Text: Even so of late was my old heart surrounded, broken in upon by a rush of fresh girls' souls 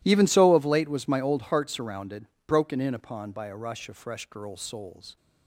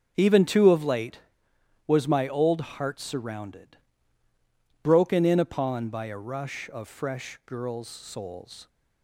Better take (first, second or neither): first